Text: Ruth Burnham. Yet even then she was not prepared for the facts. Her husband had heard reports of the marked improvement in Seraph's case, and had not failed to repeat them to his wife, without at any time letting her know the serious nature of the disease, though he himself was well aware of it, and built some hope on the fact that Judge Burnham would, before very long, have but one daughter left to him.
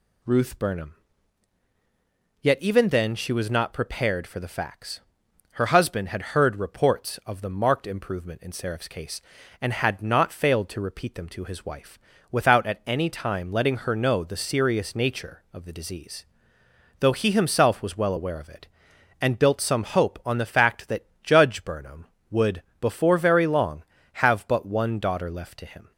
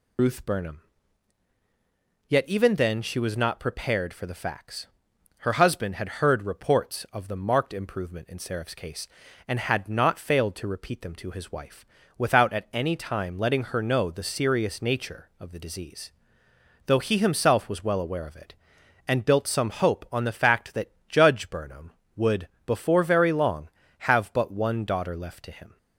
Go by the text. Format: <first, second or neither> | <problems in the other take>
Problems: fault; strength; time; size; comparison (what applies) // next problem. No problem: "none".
first | loses the start of "Ruth"; at 0.1 s; 85 ms // pauses between "that" and "Judge"; slight; at 20.9 s; 0.18 s long; slight in the first